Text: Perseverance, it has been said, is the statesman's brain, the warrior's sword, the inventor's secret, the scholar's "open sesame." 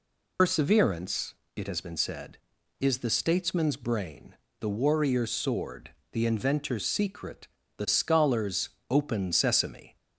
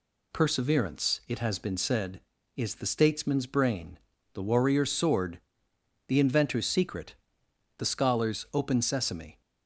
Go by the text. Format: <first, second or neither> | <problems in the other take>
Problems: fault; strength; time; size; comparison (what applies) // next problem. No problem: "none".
second | loses the start of "Perseverance"; at 0.3 s; 100 ms // pauses between "scholar's" and "open"; slight; at 8.6 s; 0.20 s long